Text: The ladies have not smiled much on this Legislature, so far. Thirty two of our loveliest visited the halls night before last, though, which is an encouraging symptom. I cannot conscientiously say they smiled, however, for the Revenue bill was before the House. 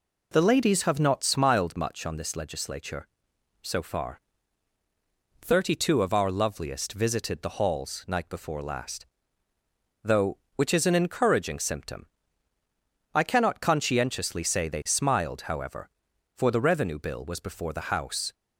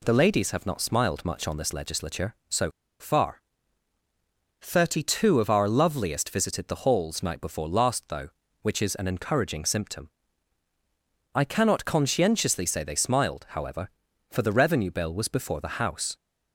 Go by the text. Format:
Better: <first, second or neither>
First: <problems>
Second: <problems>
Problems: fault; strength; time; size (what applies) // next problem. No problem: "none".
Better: first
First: none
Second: pauses between "so" and "far"; slight; at 2.7 s; 0.29 s long